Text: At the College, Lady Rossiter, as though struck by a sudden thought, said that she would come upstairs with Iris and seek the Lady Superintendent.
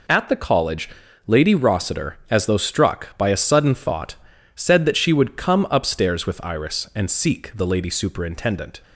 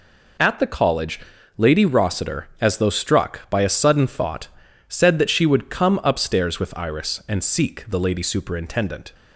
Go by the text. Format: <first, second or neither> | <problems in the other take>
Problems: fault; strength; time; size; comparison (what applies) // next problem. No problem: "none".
neither | none